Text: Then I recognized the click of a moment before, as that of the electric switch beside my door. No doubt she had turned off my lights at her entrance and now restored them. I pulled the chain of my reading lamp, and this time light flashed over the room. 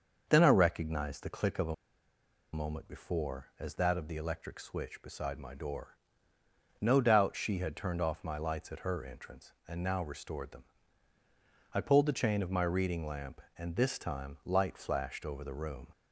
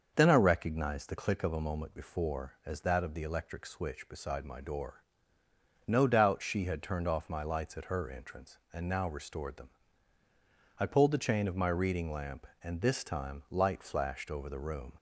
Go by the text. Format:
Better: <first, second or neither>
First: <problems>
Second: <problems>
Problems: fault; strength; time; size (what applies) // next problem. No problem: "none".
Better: second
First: starts louder than the rest; until 1.2 s; 6.5 dB // pauses between "a" and "moment"; noticeable; at 1.7 s; 0.78 s long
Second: starts louder than the rest; until 1.1 s; 6.5 dB